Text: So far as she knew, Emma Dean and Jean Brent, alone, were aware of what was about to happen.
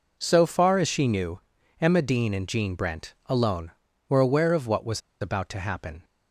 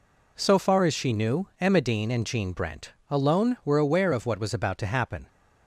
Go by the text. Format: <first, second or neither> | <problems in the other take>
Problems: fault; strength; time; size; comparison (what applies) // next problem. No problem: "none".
second | pauses between "was" and "about"; slight; at 4.9 s; 0.21 s long